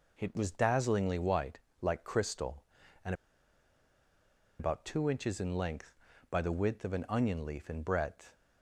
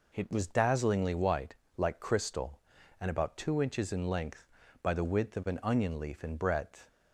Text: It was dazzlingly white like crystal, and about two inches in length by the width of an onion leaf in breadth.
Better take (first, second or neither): second